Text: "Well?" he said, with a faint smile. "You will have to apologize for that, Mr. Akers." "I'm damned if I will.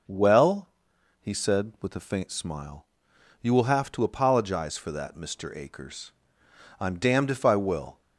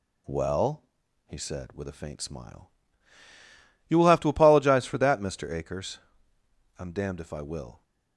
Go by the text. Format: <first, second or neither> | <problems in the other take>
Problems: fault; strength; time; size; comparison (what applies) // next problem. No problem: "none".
neither | none